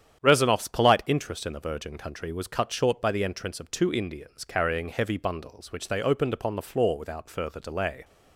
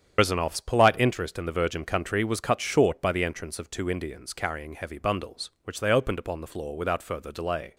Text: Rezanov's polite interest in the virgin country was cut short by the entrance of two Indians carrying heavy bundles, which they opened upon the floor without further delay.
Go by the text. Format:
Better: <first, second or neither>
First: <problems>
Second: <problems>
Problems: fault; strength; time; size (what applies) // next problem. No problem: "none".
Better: first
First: starts louder than the rest; strong; until 1.2 s; 9.5 dB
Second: loses the start of "Rezanov's"; at 0.1 s; 100 ms // starts louder than the rest; strong; until 1.2 s; 8.5 dB